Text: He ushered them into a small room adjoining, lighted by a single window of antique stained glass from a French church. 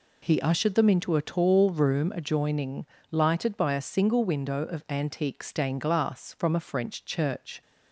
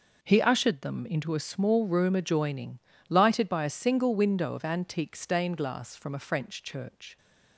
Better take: second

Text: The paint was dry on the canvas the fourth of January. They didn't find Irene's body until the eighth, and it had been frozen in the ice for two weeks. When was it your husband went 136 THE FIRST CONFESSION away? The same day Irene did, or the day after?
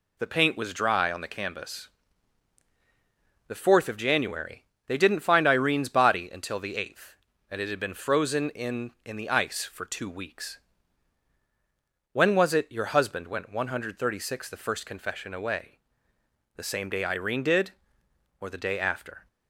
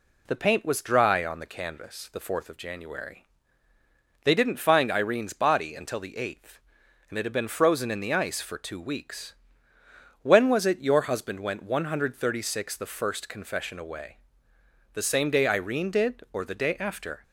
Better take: second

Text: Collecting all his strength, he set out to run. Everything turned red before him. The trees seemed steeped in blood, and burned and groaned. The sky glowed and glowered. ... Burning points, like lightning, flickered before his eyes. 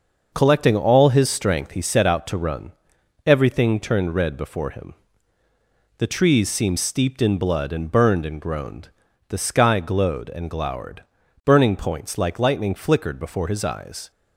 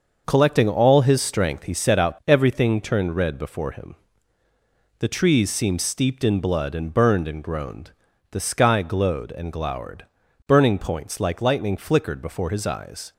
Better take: first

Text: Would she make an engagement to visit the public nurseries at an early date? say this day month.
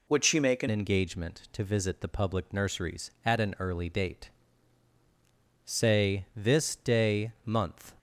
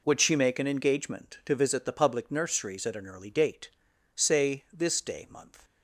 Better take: second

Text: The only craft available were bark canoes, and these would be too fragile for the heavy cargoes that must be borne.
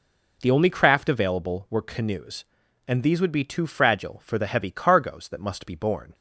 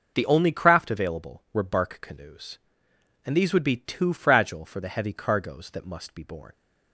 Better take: second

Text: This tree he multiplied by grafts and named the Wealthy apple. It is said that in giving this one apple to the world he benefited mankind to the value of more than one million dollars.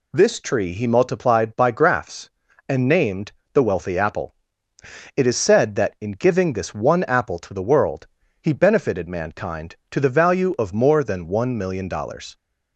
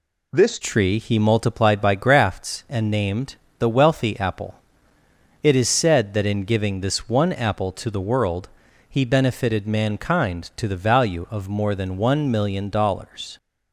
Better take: first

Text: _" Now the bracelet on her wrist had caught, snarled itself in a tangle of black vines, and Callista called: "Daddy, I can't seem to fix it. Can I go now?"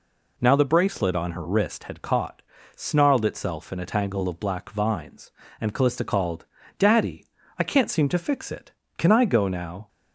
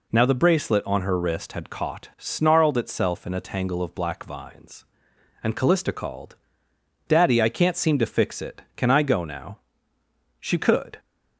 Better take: first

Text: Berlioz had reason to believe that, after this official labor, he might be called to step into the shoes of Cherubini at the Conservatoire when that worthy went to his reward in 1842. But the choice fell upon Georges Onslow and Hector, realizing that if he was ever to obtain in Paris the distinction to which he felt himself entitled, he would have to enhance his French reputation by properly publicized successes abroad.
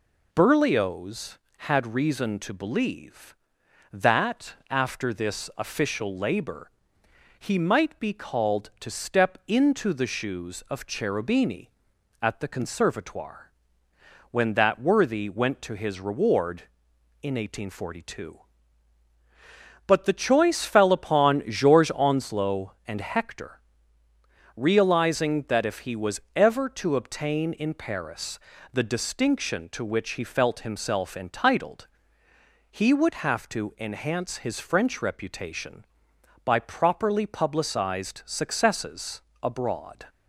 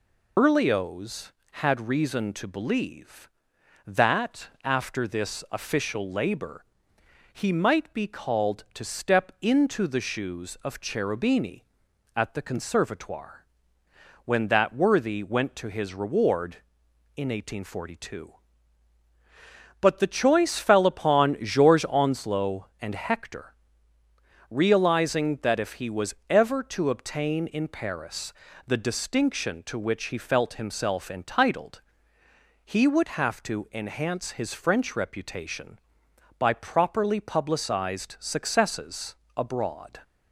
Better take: first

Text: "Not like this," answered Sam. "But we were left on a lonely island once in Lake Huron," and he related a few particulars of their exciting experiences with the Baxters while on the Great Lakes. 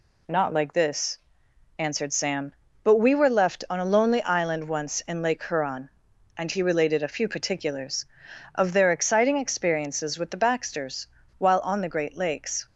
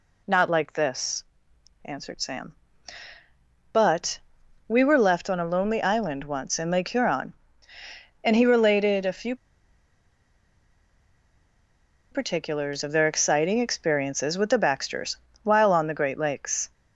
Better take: first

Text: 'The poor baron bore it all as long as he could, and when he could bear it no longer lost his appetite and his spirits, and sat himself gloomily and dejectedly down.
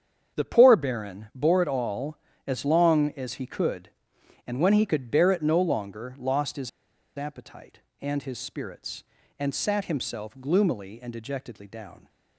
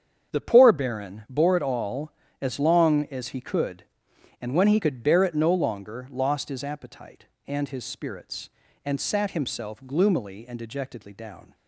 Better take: second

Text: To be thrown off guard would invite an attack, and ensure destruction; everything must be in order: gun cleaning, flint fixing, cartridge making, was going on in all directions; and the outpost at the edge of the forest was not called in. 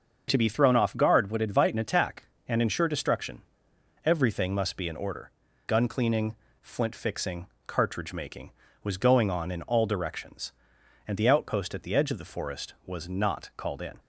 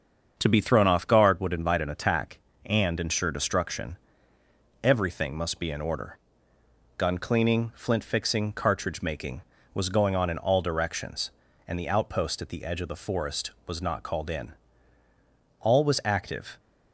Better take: first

